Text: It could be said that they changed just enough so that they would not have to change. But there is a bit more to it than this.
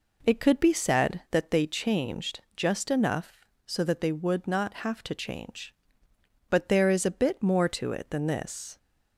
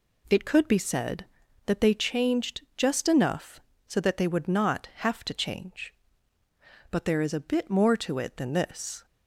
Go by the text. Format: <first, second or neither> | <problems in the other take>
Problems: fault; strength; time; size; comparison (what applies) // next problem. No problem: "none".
neither | none